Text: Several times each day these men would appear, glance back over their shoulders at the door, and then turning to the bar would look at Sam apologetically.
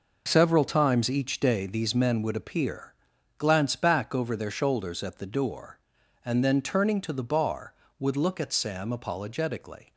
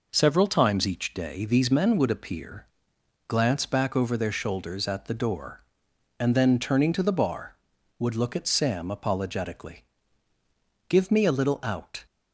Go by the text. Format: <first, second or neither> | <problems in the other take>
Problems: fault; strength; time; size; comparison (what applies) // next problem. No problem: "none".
first | goes on to say "Give me a little out"; noticeable; from 10.8 s on; 1.1 s long